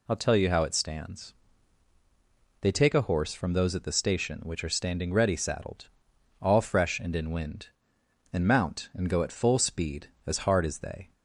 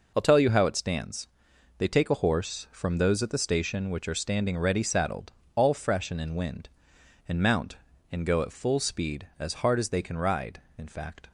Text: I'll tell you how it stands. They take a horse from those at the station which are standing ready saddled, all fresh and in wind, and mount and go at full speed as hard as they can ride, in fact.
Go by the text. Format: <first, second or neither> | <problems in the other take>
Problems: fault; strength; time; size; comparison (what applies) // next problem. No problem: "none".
second | stops before "can ride in fact"; at 11.1 s